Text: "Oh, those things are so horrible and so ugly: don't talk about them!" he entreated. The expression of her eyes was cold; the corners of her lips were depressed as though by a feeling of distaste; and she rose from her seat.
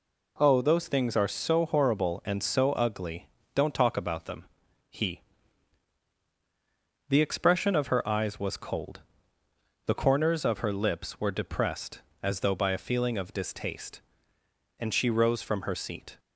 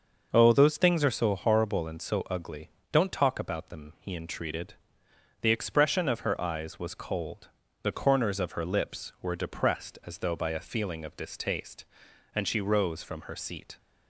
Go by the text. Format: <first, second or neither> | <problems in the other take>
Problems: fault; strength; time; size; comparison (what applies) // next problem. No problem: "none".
second | skips "entreated"; at 6.1 s